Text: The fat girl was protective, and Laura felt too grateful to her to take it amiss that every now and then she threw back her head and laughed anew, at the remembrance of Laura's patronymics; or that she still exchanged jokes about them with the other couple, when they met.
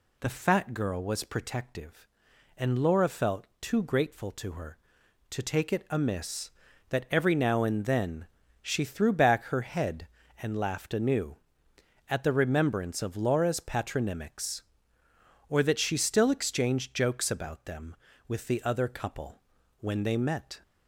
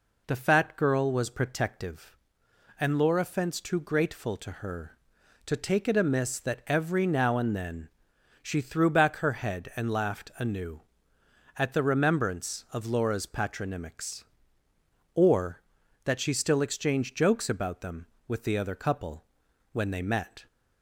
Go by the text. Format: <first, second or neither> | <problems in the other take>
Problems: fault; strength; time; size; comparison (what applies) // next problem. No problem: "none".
first | says "fence" for "felt"; at 3.2 s // pauses between "then" and "she"; noticeable; at 7.9 s; 0.50 s long; slight in the first